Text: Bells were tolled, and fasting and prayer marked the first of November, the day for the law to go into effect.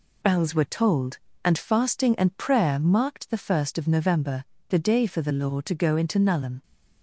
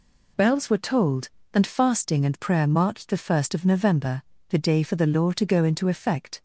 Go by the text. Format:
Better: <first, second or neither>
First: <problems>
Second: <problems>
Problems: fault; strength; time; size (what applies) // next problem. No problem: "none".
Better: second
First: says "nullum" for "effect"; at 6.1 s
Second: none